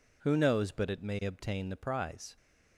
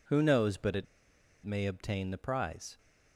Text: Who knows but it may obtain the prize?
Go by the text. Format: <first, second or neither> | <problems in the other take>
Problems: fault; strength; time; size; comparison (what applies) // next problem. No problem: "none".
first | pauses between "it" and "may"; noticeable; at 0.8 s; 0.59 s long